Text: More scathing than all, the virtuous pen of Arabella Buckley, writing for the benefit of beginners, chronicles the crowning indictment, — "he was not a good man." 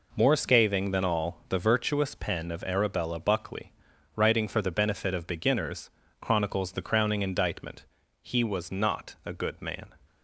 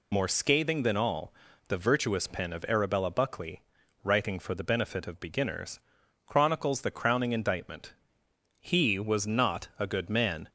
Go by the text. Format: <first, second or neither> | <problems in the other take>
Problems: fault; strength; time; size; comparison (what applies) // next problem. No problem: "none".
first | loses the start of "More"; at 0.1 s; 45 ms